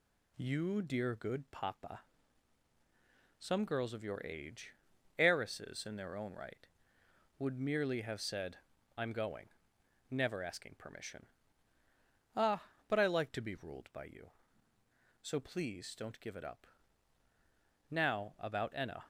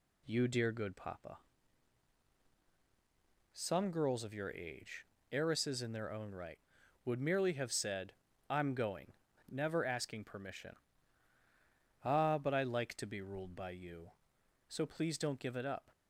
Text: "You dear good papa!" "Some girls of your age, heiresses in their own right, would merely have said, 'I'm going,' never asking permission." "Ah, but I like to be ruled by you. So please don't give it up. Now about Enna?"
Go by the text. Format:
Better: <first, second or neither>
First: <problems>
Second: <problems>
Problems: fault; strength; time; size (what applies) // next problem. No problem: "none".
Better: first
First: none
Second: stops before "Now about Enna"; at 15.9 s